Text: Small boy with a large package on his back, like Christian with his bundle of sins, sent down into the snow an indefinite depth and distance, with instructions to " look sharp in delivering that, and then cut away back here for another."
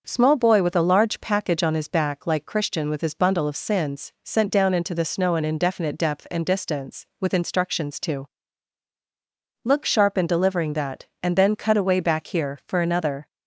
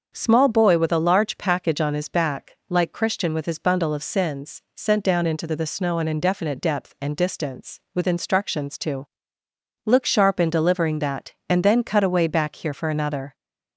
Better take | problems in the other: first | starts louder than the rest; until 1.1 s; 6.5 dB; also in the first // says "the" twice; at 5.5 s

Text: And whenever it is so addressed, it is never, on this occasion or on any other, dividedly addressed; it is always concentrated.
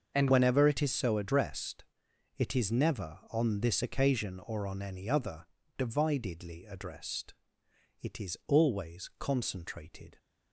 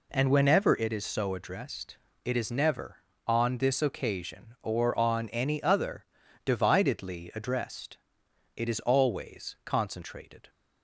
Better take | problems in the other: second | starts louder than the rest; until 1.1 s; 6.5 dB // changes voice at "whenever"; from 0.2 s on; 9.9 s long

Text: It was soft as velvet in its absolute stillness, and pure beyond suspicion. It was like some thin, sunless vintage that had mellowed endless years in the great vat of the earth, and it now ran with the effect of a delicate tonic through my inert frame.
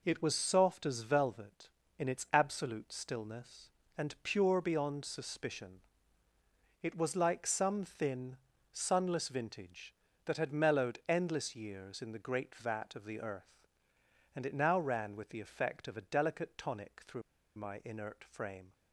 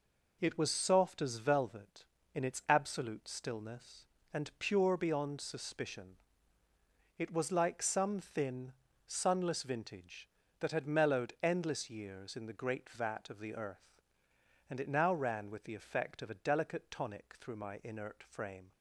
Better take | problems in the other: second | pauses between "through" and "my"; slight; at 17.2 s; 0.35 s long

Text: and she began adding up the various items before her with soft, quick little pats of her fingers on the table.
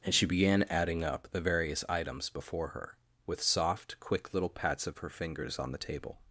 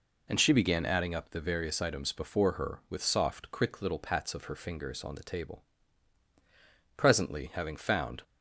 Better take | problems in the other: first | goes on to say "Presently having found"; noticeable; from 6.9 s on; 1.2 s long

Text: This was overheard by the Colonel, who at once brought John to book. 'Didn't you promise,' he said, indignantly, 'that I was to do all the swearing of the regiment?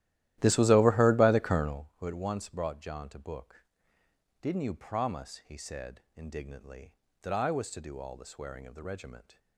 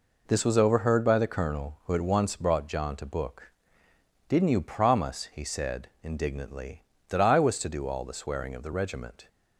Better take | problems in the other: second | starts louder than the rest; strong; until 1.9 s; 14.5 dB

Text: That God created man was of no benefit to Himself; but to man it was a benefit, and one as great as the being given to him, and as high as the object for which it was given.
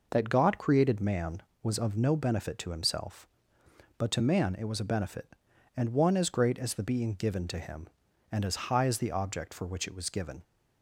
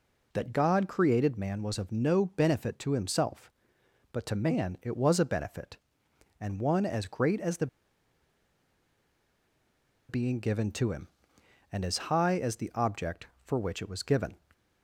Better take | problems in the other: first | pauses between "the" and "being"; strong; at 7.6 s; 2.4 s long

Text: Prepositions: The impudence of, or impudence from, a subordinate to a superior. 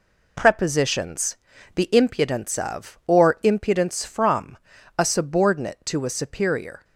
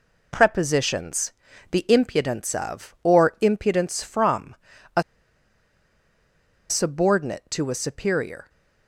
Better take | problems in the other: first | pauses between "a" and "subordinate"; strong; at 5.0 s; 1.6 s long

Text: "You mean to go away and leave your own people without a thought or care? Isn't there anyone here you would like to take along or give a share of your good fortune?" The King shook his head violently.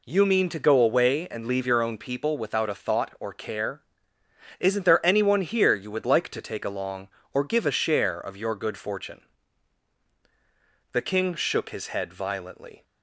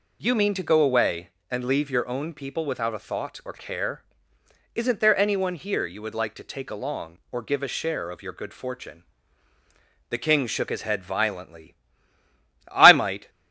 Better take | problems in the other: first | goes on to say "I might"; from 12.6 s on; 0.60 s long

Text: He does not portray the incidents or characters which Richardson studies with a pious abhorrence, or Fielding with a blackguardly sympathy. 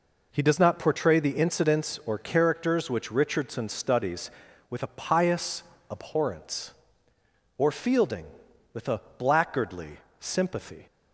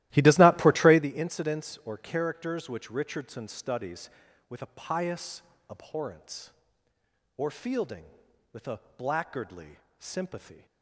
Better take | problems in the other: first | starts louder than the rest; strong; until 1.1 s; 15.5 dB // pauses between "pious" and "abhorrence"; slight; at 5.4 s; 0.28 s long; slight in the first // pauses between "a" and "blackguardly"; slight; at 8.8 s; 0.16 s long; slight in the first // pauses between "blackguardly" and "sympathy"; slight; at 9.7 s; 0.22 s long; slight in the first

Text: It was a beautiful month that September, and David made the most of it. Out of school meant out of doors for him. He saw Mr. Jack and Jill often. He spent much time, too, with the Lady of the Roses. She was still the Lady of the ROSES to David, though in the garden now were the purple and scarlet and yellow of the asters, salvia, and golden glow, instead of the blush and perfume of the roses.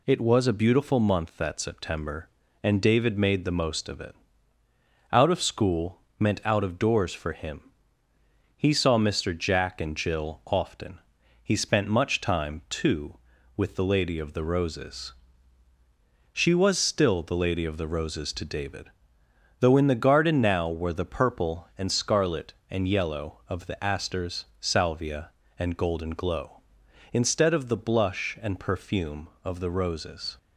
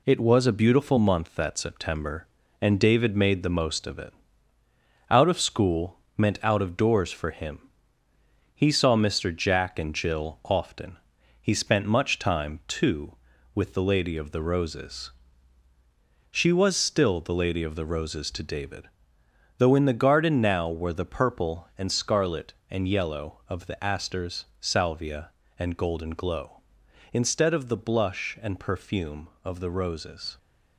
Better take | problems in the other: first | gets quieter; noticeable; throughout; 4 dB // pauses between "school" and "meant"; slight; at 5.9 s; 0.18 s long; slight in the first

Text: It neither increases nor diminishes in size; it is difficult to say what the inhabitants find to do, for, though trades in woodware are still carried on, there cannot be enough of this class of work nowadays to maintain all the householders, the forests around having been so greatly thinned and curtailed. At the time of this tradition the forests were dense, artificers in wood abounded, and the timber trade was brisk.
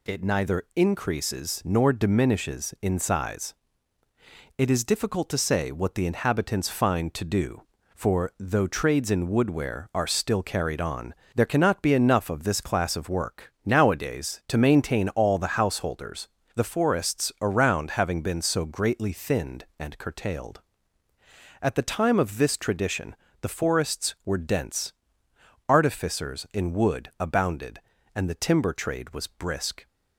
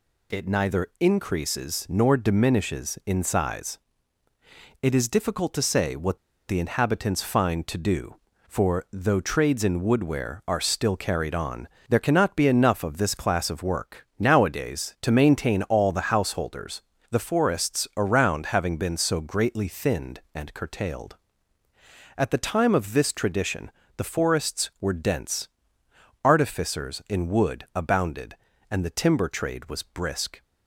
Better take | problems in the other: first | pauses between "what" and "the"; slight; at 6.1 s; 0.30 s long // pauses between "tradition" and "the"; slight; at 23.7 s; 0.26 s long; slight in the first

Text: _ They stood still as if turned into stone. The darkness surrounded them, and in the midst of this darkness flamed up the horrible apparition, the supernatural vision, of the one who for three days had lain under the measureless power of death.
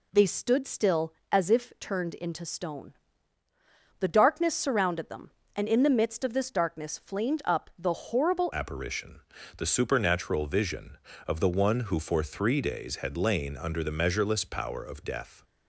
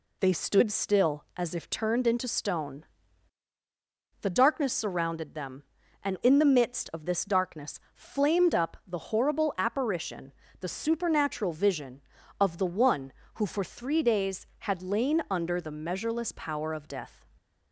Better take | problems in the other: second | changes voice at "apparition"; from 8.5 s on; 6.9 s long

